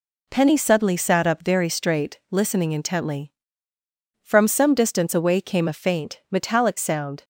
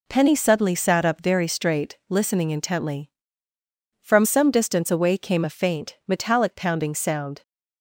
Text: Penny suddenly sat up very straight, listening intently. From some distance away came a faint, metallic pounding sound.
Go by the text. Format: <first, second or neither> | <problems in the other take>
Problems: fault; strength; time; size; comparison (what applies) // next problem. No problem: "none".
second | skips "pounding"; at 6.7 s